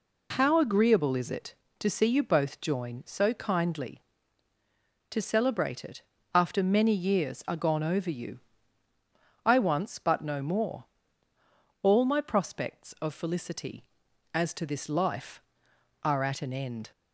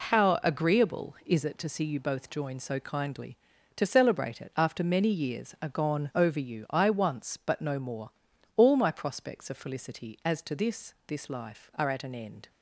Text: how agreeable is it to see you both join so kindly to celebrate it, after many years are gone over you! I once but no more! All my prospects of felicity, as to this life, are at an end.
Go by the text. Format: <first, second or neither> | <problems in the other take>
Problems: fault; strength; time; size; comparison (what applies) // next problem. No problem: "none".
first | says "this" twice; at 11.0 s